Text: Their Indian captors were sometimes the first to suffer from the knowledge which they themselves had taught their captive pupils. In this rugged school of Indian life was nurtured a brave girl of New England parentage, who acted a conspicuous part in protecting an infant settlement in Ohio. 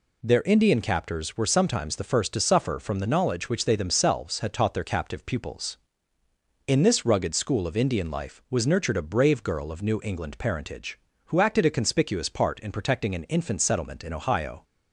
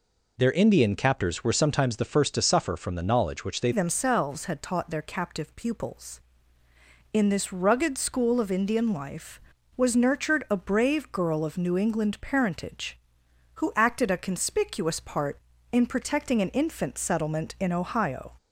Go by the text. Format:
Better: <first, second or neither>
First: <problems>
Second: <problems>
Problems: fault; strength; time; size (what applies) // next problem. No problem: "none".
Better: first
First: none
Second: changes voice at "themselves"; from 3.7 s on; 14.6 s long